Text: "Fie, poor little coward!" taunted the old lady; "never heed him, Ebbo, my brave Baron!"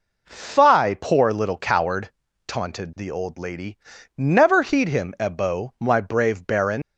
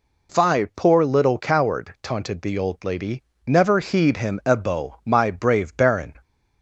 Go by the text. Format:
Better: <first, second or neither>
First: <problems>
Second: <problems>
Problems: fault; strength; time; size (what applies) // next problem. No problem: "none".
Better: second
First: leaves "Baron" unfinished; at 6.8 s; 80 ms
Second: none